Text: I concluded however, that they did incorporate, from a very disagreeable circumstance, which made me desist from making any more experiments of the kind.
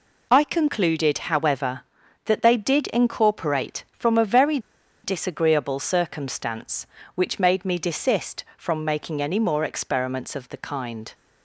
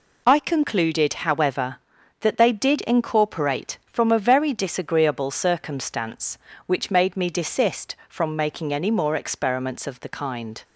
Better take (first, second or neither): second